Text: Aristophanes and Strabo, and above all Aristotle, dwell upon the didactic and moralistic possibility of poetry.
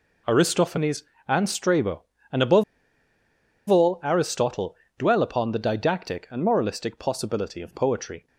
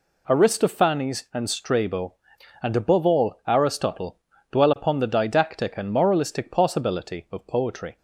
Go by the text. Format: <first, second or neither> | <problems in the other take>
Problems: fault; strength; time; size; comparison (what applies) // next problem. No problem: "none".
second | pauses between "above" and "all"; at 2.6 s; 1.0 s long